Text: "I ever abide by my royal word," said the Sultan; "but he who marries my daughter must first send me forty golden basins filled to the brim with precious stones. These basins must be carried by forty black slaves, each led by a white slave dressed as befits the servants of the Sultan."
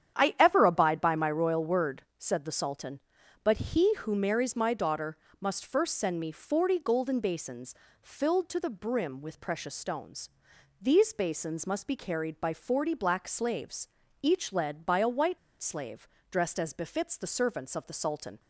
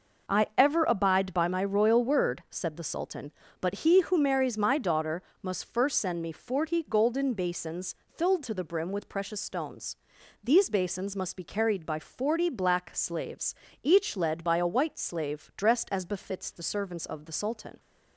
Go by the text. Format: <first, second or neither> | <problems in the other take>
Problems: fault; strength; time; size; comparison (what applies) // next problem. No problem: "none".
second | starts louder than the rest; strong; until 1.1 s; 9 dB // pauses between "daughter" and "must"; slight; at 5.1 s; 0.24 s long; slight in the second // pauses between "basins" and "filled"; slight; at 7.7 s; 0.30 s long // pauses between "white" and "slave"; slight; at 15.3 s; 0.23 s long // pauses between "slave" and "dressed"; slight; at 16.0 s; 0.24 s long